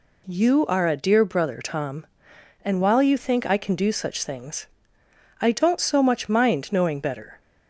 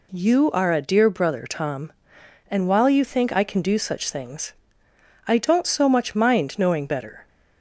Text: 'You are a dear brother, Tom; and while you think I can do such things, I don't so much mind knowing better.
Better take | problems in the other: neither | none

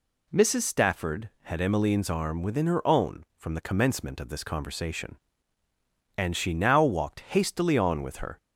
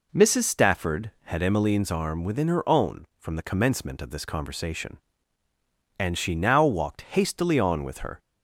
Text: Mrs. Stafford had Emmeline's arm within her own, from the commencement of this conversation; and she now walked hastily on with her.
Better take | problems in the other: first | starts louder than the rest; noticeable; until 1.7 s; 4 dB

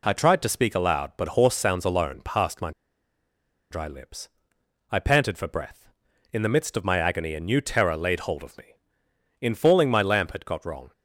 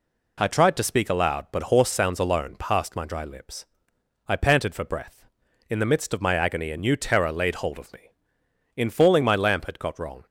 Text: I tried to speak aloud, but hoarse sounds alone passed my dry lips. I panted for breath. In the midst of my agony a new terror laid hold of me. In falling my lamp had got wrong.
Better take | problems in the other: second | pauses between "my" and "dry"; at 2.7 s; 1.0 s long

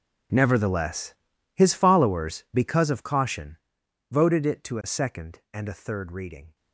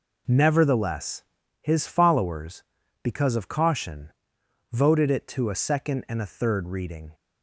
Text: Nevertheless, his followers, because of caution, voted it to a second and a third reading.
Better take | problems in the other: second | gets quieter; strong; throughout; 18.5 dB

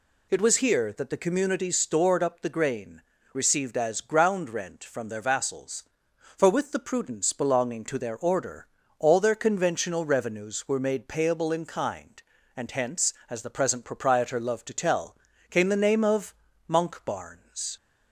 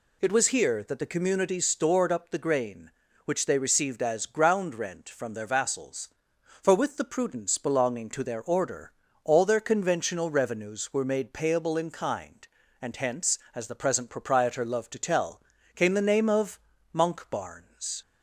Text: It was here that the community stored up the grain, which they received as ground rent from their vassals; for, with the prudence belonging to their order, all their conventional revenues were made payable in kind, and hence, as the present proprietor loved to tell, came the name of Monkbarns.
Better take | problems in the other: second | skips "which they"; at 3.1 s // pauses between "of" and "Monkbarns"; slight; at 16.3 s; 0.36 s long; slight in the second

